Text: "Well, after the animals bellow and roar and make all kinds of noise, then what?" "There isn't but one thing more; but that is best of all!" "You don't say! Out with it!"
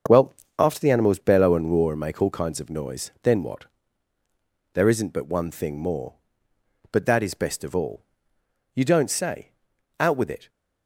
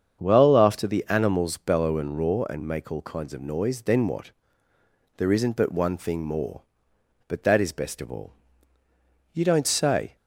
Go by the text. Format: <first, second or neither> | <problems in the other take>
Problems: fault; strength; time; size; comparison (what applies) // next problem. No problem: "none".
first | starts louder than the rest; strong; until 1.2 s; 7.5 dB; also in the first // stops before "Out with it"; at 10.1 s